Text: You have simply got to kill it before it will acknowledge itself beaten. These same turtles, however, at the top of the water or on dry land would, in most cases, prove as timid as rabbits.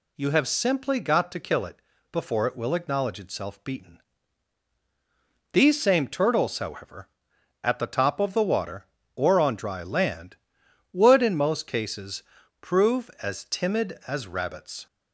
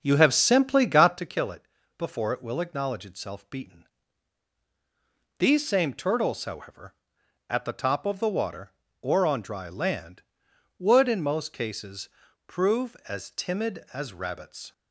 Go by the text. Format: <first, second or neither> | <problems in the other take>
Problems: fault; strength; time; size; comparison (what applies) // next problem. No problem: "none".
first | starts louder than the rest; until 1.3 s; 7 dB // pauses between "it" and "before"; slight; at 1.6 s; 0.32 s long; slight in the first